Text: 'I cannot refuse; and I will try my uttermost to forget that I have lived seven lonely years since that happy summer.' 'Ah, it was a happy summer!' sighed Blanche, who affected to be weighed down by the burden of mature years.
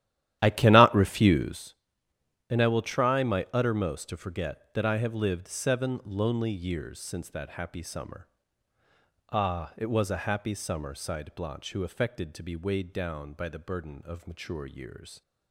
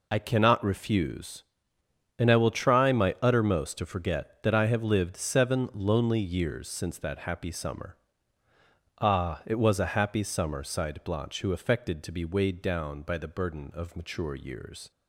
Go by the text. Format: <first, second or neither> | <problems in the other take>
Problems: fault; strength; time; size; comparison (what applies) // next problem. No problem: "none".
second | starts louder than the rest; strong; until 1.7 s; 12.5 dB